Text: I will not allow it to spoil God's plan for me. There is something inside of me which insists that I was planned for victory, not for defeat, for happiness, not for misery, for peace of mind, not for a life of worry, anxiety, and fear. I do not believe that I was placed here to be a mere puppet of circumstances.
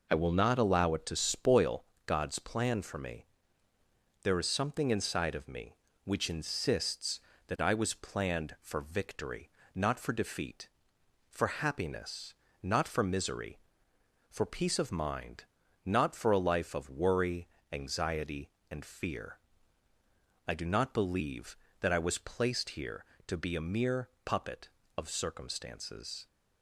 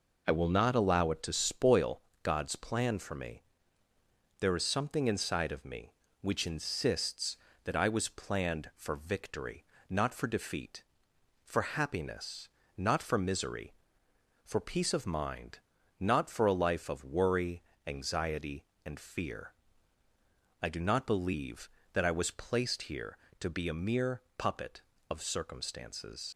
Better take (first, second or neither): first